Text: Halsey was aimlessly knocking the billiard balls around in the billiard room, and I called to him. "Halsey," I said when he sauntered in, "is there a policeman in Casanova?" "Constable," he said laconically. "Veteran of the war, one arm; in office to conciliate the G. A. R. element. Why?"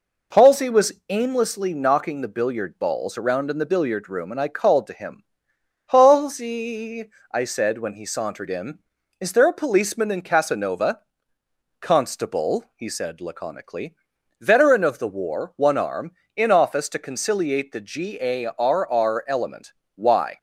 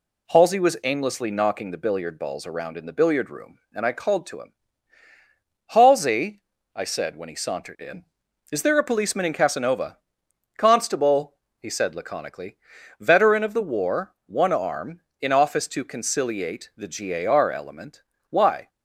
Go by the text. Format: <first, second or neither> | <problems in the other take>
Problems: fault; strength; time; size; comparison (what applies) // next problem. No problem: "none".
second | pauses between "was" and "aimlessly"; slight; at 0.9 s; 0.16 s long // says "R" twice; at 18.8 s